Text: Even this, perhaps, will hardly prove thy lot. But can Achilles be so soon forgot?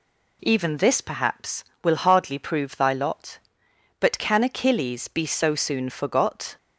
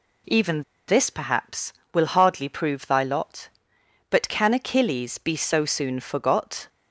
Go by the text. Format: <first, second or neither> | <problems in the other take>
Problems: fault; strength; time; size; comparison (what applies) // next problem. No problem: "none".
first | pauses between "Even" and "this"; slight; at 0.6 s; 0.25 s long